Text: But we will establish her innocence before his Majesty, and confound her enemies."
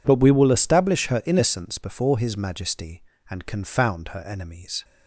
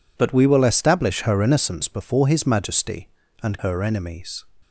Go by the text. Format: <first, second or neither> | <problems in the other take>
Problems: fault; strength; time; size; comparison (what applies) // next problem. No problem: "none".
first | skips "confound"; at 3.5 s